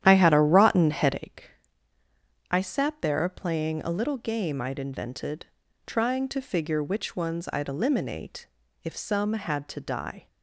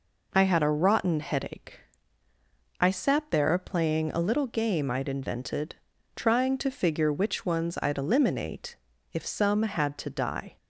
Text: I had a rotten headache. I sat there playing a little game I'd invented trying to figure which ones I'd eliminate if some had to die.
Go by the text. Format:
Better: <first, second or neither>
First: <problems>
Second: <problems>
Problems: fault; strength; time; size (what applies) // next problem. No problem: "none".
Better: second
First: starts louder than the rest; strong; until 1.3 s; 11 dB // pauses between "invented" and "trying"; at 5.4 s; 0.40 s long // pauses between "eliminate" and "if"; at 8.4 s; 0.38 s long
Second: pauses between "invented" and "trying"; at 5.7 s; 0.40 s long // pauses between "eliminate" and "if"; at 8.7 s; 0.38 s long